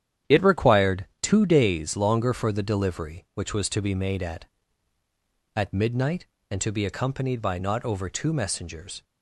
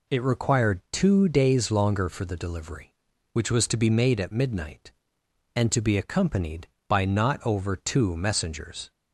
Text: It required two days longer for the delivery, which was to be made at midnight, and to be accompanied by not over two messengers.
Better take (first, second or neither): second